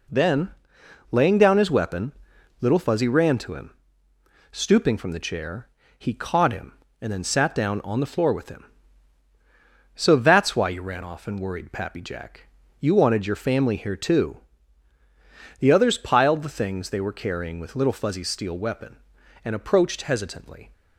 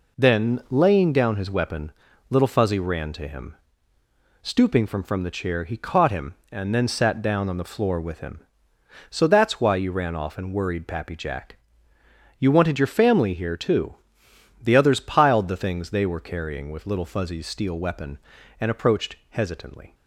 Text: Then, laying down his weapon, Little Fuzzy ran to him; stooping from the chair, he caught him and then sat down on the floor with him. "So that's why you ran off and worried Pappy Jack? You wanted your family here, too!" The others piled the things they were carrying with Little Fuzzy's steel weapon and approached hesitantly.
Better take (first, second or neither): first